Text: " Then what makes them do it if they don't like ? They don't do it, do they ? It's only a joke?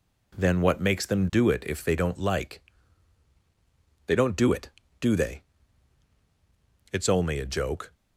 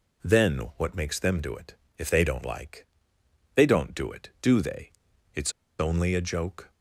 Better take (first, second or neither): first